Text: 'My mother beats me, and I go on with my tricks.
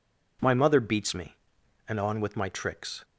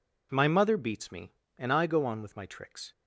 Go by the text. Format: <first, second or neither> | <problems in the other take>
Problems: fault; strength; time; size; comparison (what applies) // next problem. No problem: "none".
second | skips "I go"; at 1.9 s